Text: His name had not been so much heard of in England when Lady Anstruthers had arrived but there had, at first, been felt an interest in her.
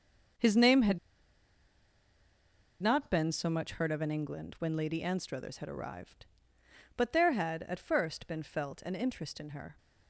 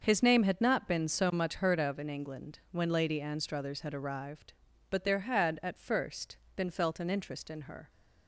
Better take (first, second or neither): second